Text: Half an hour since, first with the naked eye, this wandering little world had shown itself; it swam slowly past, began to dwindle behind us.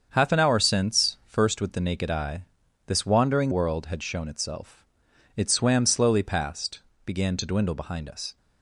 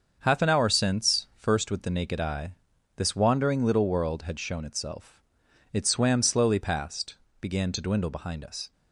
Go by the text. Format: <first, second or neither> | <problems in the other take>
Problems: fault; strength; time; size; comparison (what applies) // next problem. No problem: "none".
second | starts louder than the rest; until 1.1 s; 7 dB; also in the second // skips "little"; at 3.5 s